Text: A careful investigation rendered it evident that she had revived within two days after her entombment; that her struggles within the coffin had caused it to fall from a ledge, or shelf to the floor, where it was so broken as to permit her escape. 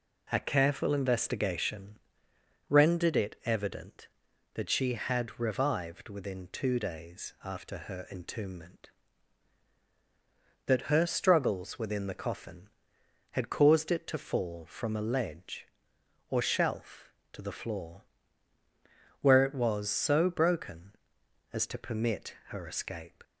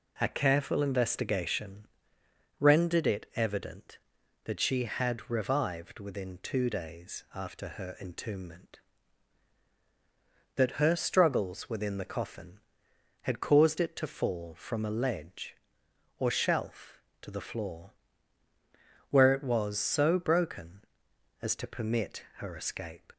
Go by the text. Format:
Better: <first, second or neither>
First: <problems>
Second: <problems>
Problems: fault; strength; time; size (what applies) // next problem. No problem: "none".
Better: neither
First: pauses between "investigation" and "rendered"; noticeable; at 1.9 s; 0.70 s long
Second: pauses between "investigation" and "rendered"; noticeable; at 1.8 s; 0.72 s long